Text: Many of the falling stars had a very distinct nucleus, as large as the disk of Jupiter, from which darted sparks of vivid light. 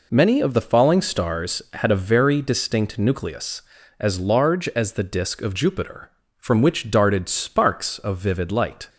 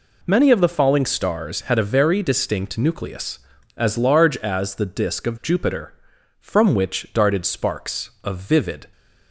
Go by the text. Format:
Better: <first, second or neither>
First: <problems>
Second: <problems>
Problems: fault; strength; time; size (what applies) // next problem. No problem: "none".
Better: first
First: none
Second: stops before "light"; at 8.9 s